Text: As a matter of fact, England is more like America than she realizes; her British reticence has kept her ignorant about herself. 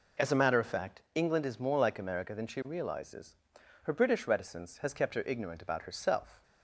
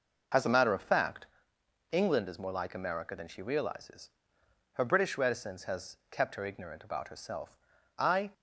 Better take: first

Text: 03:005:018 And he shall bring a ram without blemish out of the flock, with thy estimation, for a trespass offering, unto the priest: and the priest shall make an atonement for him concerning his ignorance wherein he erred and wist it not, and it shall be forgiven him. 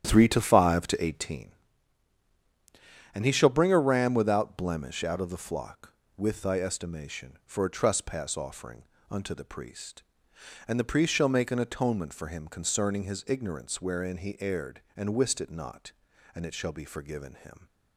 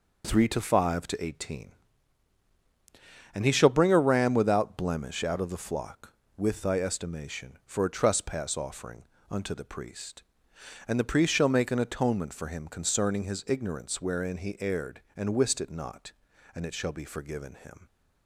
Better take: second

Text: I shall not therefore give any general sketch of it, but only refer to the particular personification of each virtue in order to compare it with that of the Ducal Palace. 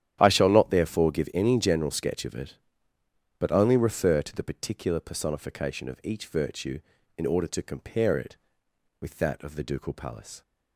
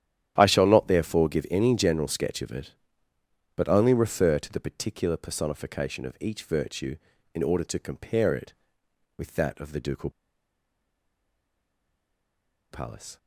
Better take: first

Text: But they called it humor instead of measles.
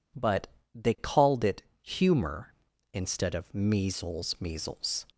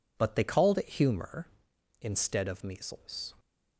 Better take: second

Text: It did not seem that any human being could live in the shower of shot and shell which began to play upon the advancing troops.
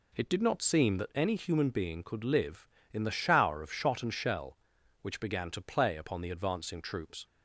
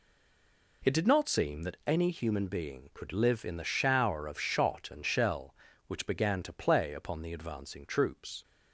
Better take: first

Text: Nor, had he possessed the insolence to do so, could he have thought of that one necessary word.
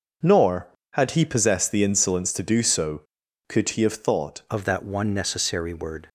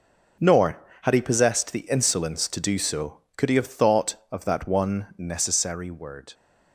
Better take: second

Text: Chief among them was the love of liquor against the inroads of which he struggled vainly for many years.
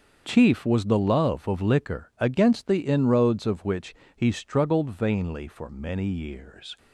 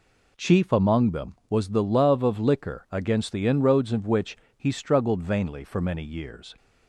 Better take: second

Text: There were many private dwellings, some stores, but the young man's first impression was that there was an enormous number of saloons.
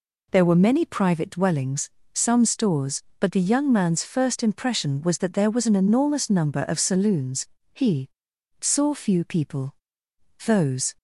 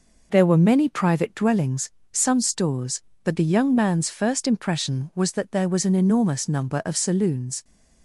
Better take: second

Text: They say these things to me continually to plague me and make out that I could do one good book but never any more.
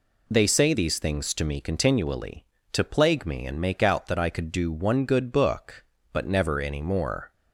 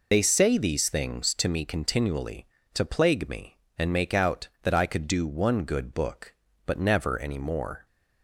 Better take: first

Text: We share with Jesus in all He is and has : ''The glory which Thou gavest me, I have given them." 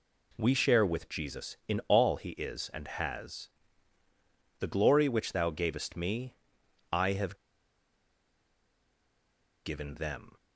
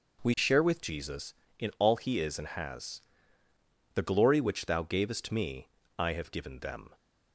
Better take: second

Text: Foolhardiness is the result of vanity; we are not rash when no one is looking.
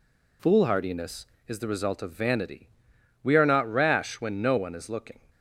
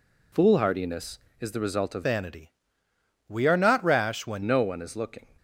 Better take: first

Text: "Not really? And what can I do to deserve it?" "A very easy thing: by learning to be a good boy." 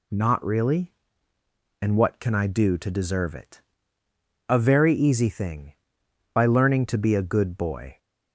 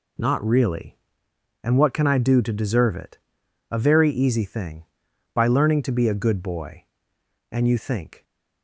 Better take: first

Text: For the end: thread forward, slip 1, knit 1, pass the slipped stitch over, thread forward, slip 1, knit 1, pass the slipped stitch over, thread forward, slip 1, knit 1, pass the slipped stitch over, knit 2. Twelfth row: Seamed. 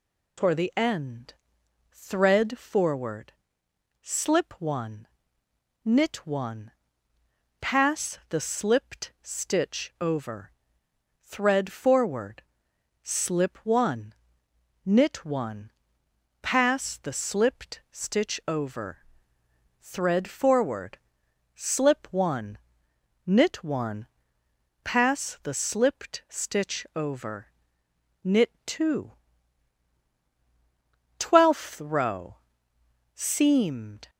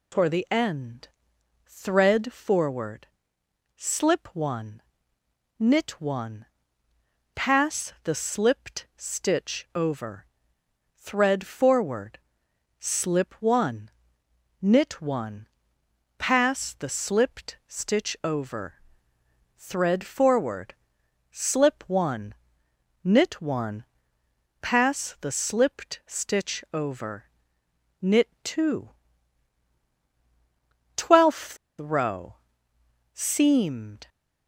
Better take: first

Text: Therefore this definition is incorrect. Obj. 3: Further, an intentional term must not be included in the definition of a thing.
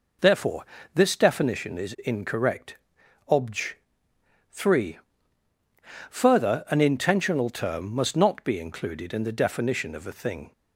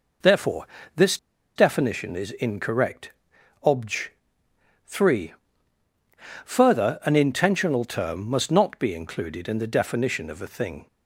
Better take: first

